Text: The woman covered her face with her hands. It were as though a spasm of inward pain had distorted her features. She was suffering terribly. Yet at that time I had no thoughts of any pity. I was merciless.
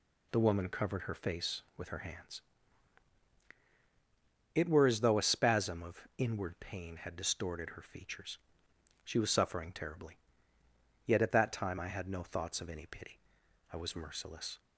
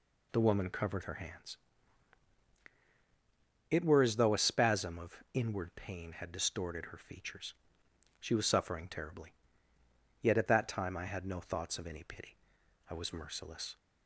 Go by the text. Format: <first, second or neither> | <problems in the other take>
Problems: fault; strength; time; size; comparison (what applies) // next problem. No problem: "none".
first | skips "her face with"; at 1.0 s